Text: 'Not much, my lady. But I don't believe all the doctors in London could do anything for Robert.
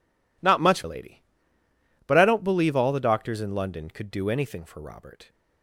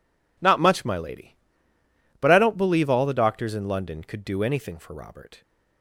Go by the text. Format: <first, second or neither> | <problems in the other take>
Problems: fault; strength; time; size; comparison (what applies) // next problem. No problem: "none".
second | skips "my"; at 0.8 s